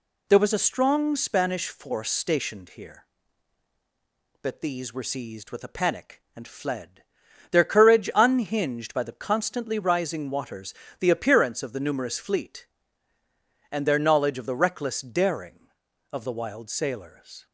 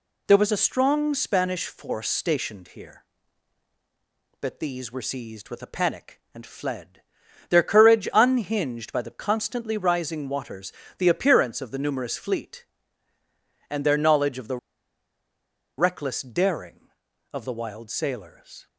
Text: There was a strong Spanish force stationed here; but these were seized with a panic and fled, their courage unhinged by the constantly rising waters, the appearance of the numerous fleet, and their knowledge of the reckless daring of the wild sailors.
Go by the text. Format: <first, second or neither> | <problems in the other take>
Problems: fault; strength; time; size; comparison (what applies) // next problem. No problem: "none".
first | pauses between "the" and "reckless"; at 14.5 s; 1.2 s long